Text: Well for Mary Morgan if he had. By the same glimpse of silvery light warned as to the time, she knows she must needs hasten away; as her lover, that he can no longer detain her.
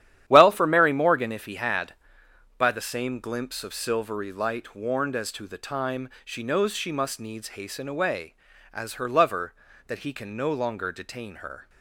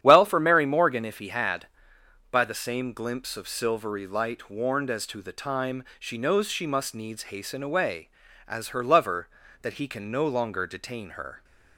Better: second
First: gets quieter; strong; throughout; 10 dB // starts louder than the rest; strong; until 1.2 s; 11 dB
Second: starts louder than the rest; strong; until 1.0 s; 10 dB

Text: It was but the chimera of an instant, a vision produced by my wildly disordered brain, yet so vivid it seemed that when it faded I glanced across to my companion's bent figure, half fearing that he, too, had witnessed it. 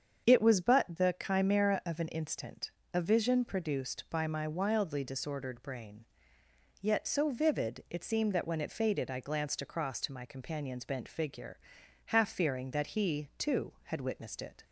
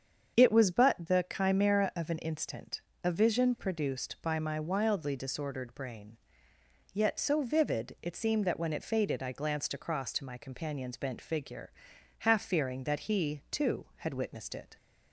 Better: neither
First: starts louder than the rest; strong; until 1.3 s; 7.5 dB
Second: starts louder than the rest; strong; until 1.4 s; 7.5 dB

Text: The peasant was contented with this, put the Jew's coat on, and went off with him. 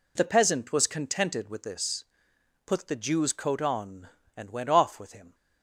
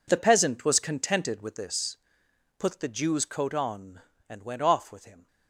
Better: first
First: none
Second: gets quieter; strong; throughout; 14 dB

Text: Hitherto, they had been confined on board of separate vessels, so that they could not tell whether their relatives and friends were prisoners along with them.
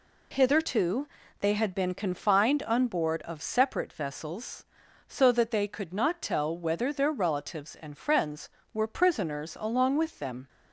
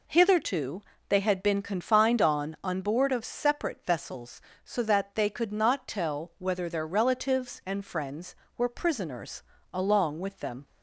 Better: first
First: none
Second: says "on" twice; at 2.6 s // pauses between "prisoners" and "along"; slight; at 9.4 s; 0.30 s long

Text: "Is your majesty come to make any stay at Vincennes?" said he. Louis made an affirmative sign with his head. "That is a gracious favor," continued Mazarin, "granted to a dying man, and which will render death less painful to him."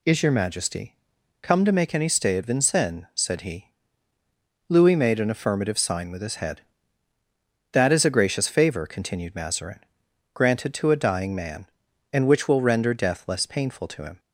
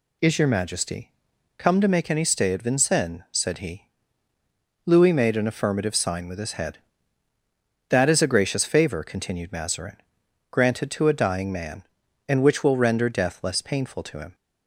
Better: neither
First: pauses between "majesty" and "come"; at 0.9 s; 0.44 s long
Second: pauses between "majesty" and "come"; at 1.1 s; 0.44 s long

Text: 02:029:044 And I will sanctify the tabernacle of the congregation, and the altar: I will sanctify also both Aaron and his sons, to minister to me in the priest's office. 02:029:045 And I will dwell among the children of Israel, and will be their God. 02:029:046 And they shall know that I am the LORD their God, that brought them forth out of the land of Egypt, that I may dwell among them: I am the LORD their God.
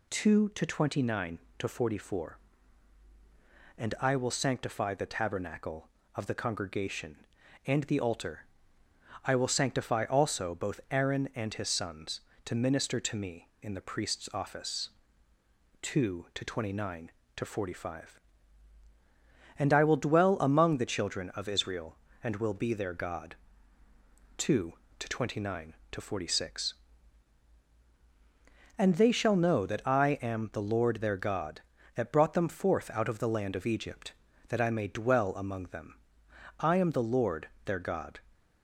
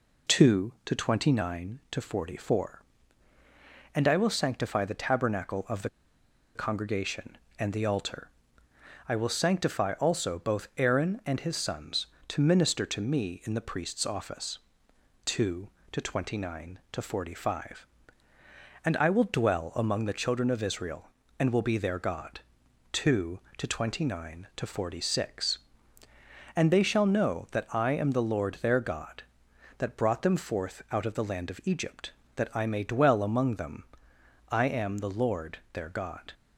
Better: first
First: pauses between "LORD" and "their"; slight; at 37.4 s; 0.16 s long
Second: pauses between "the" and "congregation"; noticeable; at 5.8 s; 0.66 s long // pauses between "LORD" and "their"; slight; at 35.5 s; 0.16 s long

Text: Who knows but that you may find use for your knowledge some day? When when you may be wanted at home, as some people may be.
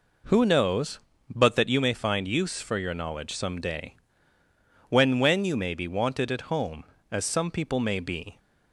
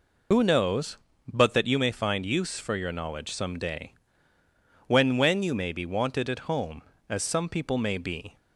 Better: first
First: none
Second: loses the start of "Who"; at 0.3 s; 90 ms

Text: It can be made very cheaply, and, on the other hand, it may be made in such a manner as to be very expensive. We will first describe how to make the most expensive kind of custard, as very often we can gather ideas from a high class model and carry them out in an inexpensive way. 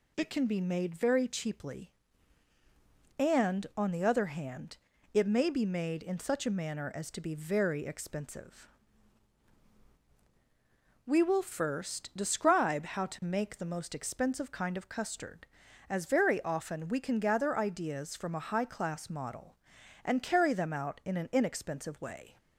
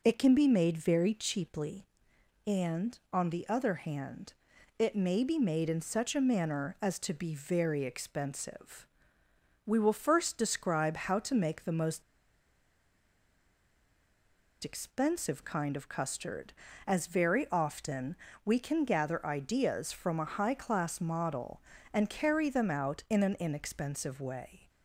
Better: first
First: none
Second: pauses between "most" and "expensive"; strong; at 12.0 s; 2.6 s long // pauses between "often" and "we"; slight; at 18.1 s; 0.28 s long

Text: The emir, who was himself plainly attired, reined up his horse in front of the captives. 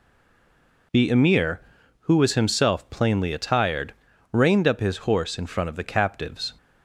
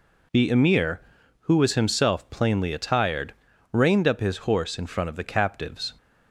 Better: second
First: stays silent before the first word; slight; until 0.9 s; 0.9 s long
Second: none

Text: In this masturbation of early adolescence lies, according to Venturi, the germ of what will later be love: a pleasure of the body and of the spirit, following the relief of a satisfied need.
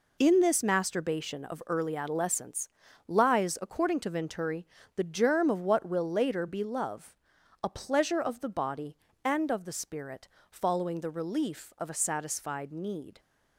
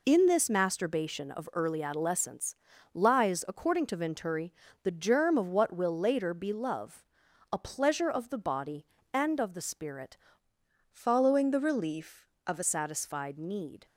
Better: first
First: pauses between "adolescence" and "lies"; slight; at 2.6 s; 0.36 s long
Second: pauses between "adolescence" and "lies"; slight; at 2.5 s; 0.36 s long // changes voice from "following" to "a"; from 10.9 to 12.6 s; 1.7 s long

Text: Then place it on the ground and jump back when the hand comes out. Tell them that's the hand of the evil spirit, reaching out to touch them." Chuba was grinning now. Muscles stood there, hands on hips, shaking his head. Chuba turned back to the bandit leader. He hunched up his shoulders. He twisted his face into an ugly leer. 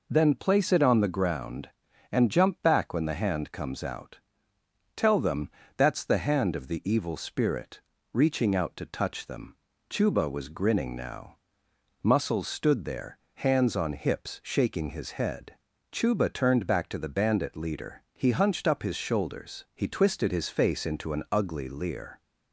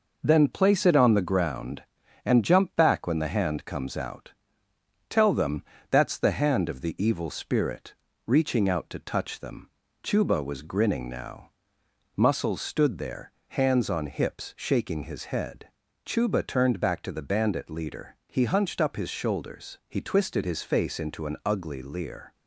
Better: first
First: pauses between "them" and "that's"; slight; at 5.4 s; 0.26 s long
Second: gets quieter; noticeable; throughout; 4.5 dB // pauses between "them" and "that's"; slight; at 5.6 s; 0.26 s long

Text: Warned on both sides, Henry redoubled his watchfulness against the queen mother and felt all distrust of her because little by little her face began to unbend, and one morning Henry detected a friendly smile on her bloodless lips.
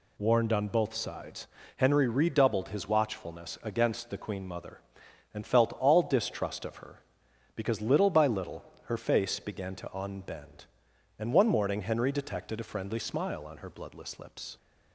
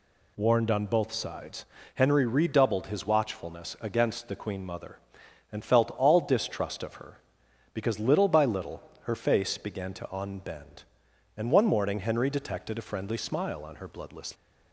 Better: first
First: pauses between "little" and "her"; slight; at 8.6 s; 0.20 s long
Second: pauses between "little" and "her"; slight; at 8.8 s; 0.20 s long // stops before "lips"; at 14.3 s

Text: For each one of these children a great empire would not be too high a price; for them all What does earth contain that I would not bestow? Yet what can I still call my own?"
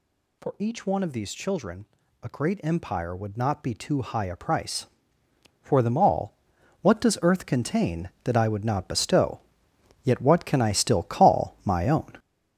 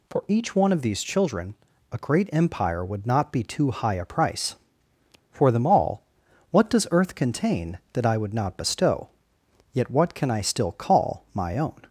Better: second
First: gets louder; throughout; 7 dB // pauses between "children" and "a"; slight; at 1.8 s; 0.36 s long // pauses between "all" and "What"; noticeable; at 6.3 s; 0.48 s long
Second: pauses between "children" and "a"; slight; at 1.5 s; 0.36 s long // pauses between "all" and "What"; noticeable; at 6.0 s; 0.48 s long

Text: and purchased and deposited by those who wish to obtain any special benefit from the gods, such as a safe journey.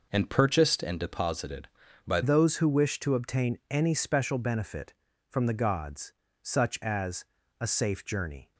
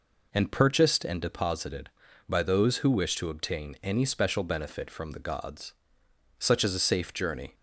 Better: second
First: changes voice at "those"; from 2.2 s on; 6.3 s long // pauses between "as" and "a"; slight; at 7.2 s; 0.36 s long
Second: none

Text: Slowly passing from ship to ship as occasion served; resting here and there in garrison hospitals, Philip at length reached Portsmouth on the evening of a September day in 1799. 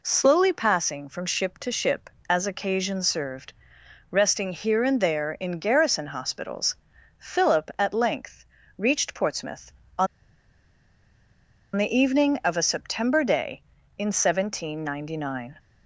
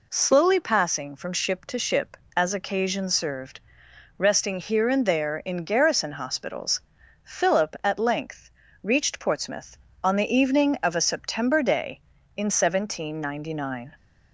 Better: second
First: pauses between "length" and "reached"; slight; at 8.4 s; 0.34 s long // pauses between "on" and "the"; strong; at 10.0 s; 1.6 s long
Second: pauses between "length" and "reached"; slight; at 8.4 s; 0.34 s long

